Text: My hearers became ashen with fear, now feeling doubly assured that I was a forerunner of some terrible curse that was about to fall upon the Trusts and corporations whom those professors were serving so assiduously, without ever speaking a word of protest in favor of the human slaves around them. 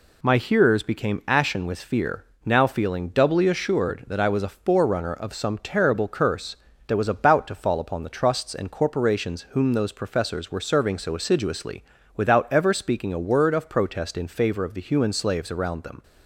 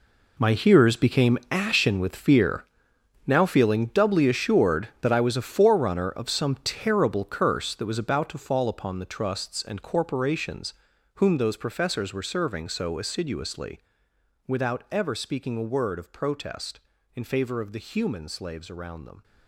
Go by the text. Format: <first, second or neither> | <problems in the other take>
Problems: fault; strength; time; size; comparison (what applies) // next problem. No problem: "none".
first | gets quieter; strong; throughout; 13.5 dB // pauses between "corporations" and "whom"; at 10.7 s; 0.40 s long